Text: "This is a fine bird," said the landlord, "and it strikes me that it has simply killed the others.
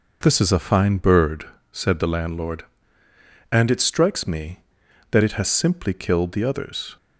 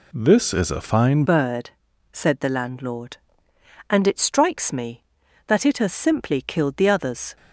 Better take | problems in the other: first | changes voice at "bird"; from 1.2 s on; 6.1 s long

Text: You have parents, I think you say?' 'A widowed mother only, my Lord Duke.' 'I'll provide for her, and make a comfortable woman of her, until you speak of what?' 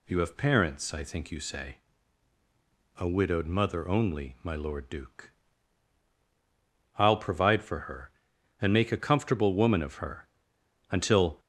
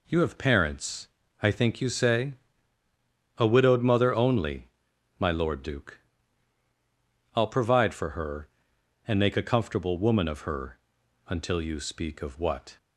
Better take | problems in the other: second | stops before "you speak of what"; at 11.3 s

